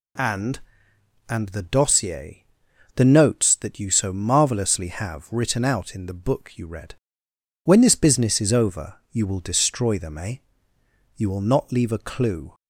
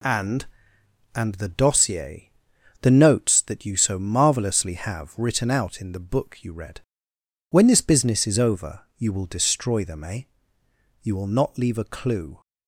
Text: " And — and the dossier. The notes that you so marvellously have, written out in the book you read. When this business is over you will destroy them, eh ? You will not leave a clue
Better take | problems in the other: first | gets quieter; noticeable; throughout; 4.5 dB // pauses between "over" and "you"; slight; at 8.8 s; 0.18 s long; slight in the first

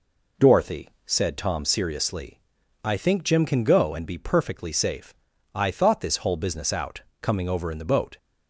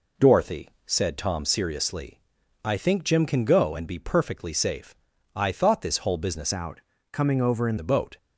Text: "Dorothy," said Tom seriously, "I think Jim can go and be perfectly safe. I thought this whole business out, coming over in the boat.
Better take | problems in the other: first | changes voice from "out" to "in"; from 6.5 to 7.7 s; 1.2 s long

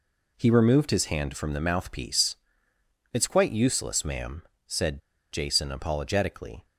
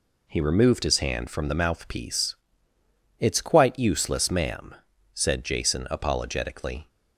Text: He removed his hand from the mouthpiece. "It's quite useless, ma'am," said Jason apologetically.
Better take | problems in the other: second | pauses between "said" and "Jason"; slight; at 5.0 s; 0.31 s long

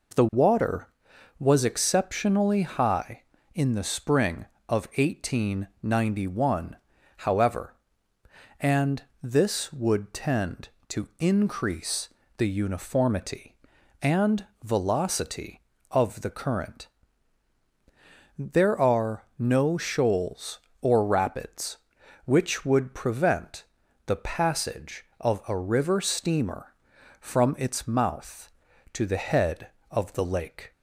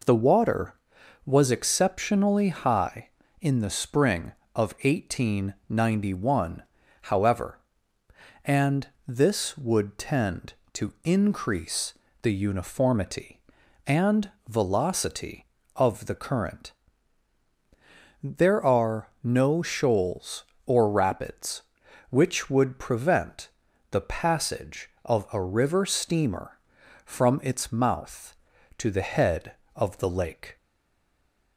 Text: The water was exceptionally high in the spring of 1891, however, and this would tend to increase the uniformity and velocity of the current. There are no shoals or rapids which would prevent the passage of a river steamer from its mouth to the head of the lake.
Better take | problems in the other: first | pauses between "and" and "this"; slight; at 8.8 s; 0.20 s long; slight in the first // pauses between "increase" and "the"; slight; at 11.9 s; 0.30 s long; slight in the first // pauses between "and" and "velocity"; slight; at 14.3 s; 0.18 s long; slight in the first // pauses between "prevent" and "the"; at 23.4 s; 0.42 s long; also in the first // stays silent after the last word; from 30.5 s on; 1.0 s long

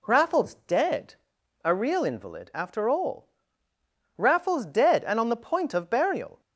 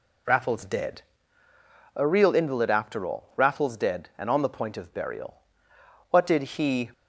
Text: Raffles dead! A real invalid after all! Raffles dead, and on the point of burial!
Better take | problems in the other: first | goes on to say "What did he"; noticeable; from 6.1 s on; 0.80 s long

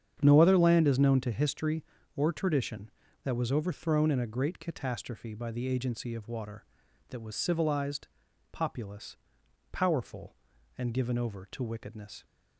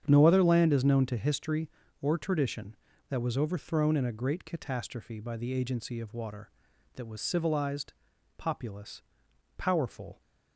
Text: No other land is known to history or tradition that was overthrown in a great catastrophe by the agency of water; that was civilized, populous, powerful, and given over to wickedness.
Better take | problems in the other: first | starts louder than the rest; strong; until 1.0 s; 8 dB; strong in the first // stops before "and given over to wickedness"; at 10.1 s

